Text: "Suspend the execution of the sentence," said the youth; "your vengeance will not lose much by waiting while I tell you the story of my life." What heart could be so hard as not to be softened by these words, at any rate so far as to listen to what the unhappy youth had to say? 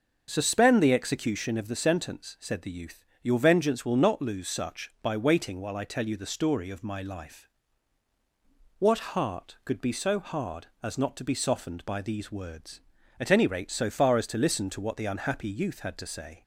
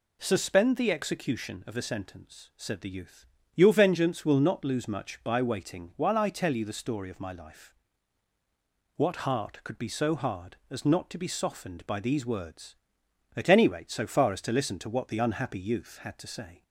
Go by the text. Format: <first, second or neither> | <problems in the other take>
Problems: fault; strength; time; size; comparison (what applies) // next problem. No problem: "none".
second | starts louder than the rest; until 1.2 s; 6.5 dB // says "such" for "much"; at 4.4 s